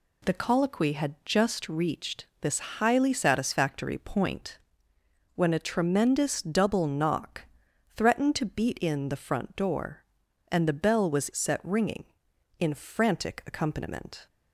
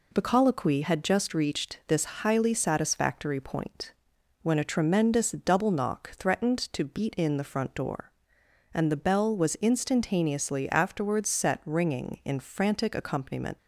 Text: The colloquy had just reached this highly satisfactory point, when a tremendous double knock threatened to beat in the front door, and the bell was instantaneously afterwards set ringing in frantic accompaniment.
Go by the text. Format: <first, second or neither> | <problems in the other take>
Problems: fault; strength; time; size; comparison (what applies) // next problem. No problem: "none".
second | pauses between "knock" and "threatened"; noticeable; at 7.4 s; 0.54 s long // skips "instantaneously afterwards"; at 11.3 s